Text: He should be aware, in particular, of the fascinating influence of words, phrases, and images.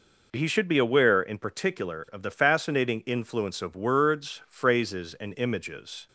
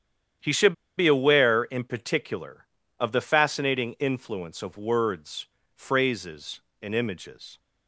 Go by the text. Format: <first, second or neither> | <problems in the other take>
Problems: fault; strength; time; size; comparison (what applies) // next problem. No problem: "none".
first | starts louder than the rest; strong; until 1.6 s; 9.5 dB // pauses between "should" and "be"; slight; at 0.7 s; 0.25 s long